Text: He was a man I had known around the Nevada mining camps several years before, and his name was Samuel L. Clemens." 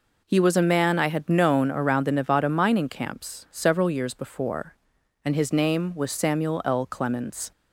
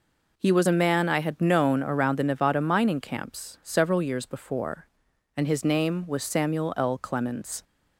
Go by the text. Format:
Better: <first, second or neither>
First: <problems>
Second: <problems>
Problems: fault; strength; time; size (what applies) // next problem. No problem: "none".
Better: neither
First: none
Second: none